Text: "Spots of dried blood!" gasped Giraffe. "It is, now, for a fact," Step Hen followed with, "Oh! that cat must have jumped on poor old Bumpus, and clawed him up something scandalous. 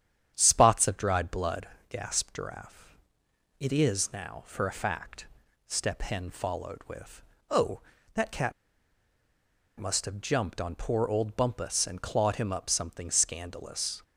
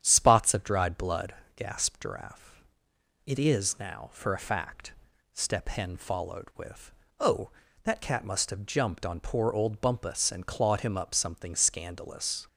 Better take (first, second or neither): second